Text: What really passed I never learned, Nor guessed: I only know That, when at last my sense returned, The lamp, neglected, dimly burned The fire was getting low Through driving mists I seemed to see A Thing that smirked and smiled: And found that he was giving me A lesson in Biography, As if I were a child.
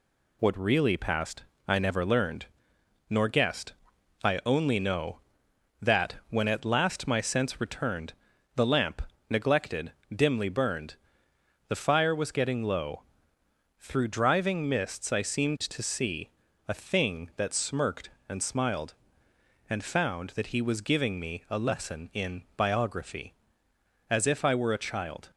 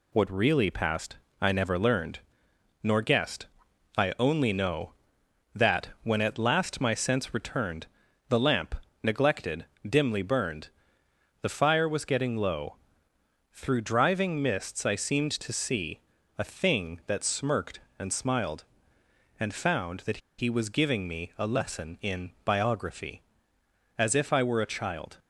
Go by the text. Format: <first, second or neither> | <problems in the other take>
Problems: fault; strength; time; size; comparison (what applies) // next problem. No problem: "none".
first | pauses between "passed" and "I"; slight; at 1.1 s; 0.24 s long; slight in the first // pauses between "burned" and "The"; noticeable; at 10.6 s; 0.74 s long; noticeable in the first // pauses between "low" and "Through"; noticeable; at 12.7 s; 0.78 s long; noticeable in the first // pauses between "see" and "A"; at 15.9 s; 0.38 s long; also in the first // pauses between "that" and "he"; slight; at 20.1 s; 0.21 s long